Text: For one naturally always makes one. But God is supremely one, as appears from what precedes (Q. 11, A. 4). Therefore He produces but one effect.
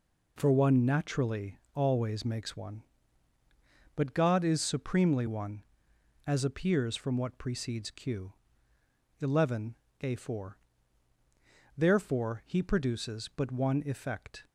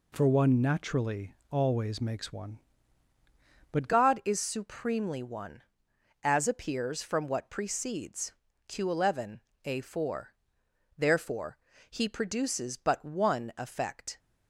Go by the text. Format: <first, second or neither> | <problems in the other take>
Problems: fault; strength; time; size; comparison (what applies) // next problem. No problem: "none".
first | pauses between "naturally" and "always"; slight; at 1.3 s; 0.16 s long; slight in the first // changes voice at "God"; from 3.8 s on; 10.3 s long // pauses between "Therefore" and "He"; slight; at 11.5 s; 0.32 s long